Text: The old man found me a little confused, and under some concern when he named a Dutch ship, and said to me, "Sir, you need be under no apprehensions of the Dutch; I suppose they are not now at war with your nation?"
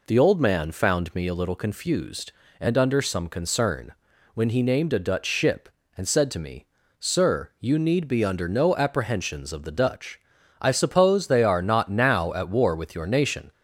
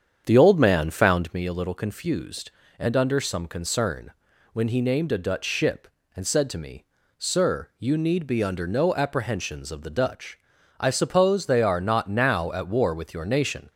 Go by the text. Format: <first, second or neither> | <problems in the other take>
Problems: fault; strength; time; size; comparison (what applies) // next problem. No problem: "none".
first | starts louder than the rest; strong; until 1.3 s; 8 dB // pauses between "concern" and "when"; at 4.1 s; 0.40 s long; also in the first